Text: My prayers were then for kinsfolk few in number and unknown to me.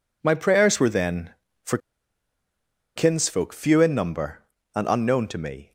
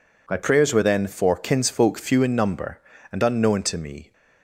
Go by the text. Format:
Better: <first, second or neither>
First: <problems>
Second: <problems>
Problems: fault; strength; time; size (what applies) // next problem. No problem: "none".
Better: second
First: pauses between "for" and "kinsfolk"; at 1.7 s; 1.1 s long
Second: none